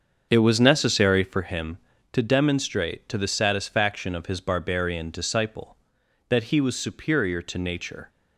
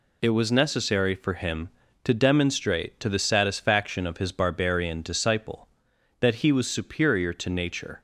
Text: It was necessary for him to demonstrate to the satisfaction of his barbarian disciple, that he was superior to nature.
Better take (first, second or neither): second